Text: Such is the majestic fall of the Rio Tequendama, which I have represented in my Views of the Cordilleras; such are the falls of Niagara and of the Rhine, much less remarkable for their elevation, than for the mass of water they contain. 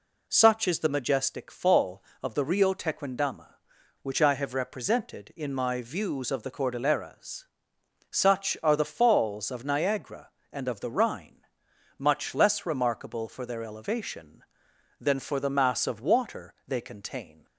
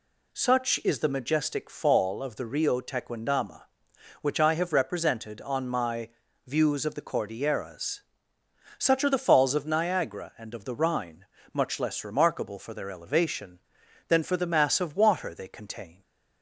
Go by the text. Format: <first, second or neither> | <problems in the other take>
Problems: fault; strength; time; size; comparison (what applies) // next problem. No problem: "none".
first | says "on" for "in"; at 5.4 s // pauses between "my" and "Views"; at 6.0 s; 0.38 s long